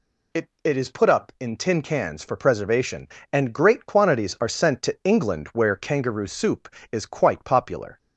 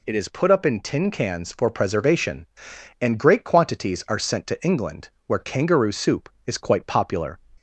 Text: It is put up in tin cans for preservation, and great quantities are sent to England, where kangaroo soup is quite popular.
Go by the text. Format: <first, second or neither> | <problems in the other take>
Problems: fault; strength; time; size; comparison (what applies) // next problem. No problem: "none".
second | says "It" twice; at 0.6 s